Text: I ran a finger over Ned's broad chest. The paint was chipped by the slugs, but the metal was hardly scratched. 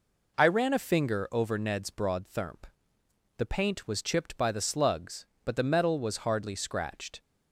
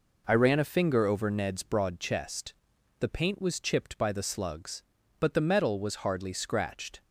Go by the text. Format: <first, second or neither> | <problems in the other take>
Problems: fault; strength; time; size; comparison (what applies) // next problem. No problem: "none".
second | says "thermp" for "chest"; at 2.2 s